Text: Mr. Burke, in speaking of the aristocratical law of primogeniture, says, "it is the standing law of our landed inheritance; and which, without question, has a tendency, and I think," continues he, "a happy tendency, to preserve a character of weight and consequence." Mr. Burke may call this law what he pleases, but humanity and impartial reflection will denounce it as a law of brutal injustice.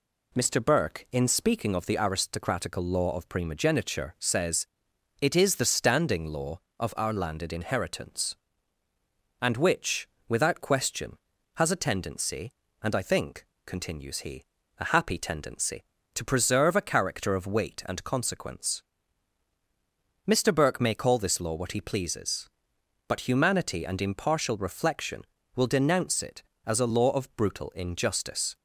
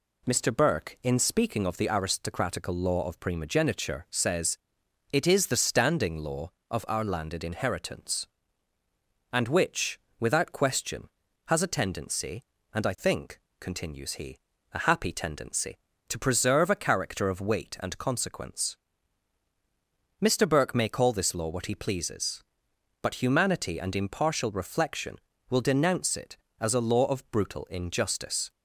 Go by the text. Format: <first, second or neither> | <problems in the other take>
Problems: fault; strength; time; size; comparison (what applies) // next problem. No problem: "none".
neither | none